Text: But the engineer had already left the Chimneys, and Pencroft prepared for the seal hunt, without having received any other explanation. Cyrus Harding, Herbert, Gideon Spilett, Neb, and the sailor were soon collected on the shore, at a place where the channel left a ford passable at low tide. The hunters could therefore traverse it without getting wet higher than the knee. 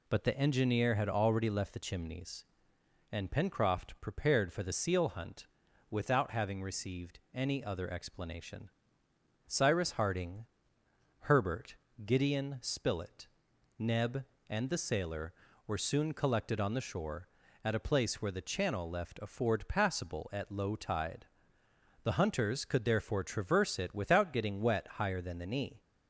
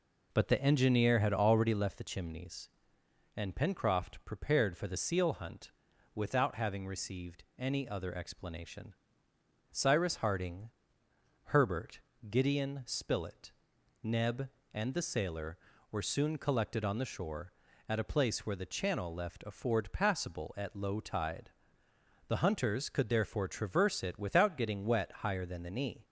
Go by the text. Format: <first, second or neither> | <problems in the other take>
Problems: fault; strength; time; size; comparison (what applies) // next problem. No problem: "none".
first | starts louder than the rest; noticeable; until 2.0 s; 4 dB // pauses between "received" and "any"; slight; at 7.4 s; 0.16 s long; slight in the first